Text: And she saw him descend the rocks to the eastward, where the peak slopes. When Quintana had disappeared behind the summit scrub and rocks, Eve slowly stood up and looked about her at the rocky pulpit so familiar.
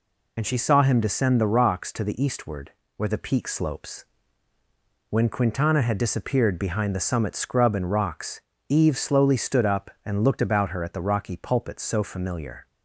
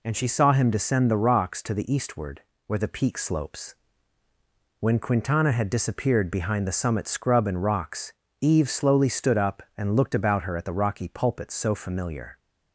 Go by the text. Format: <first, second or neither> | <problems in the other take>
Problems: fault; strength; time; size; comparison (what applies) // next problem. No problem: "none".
second | loses the start of "And"; at 0.3 s; 35 ms